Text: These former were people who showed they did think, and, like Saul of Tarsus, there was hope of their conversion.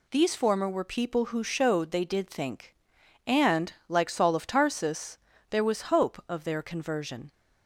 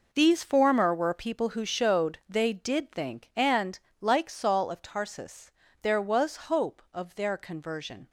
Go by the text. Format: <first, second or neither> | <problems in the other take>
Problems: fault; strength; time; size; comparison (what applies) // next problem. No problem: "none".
first | gets quieter; strong; throughout; 12 dB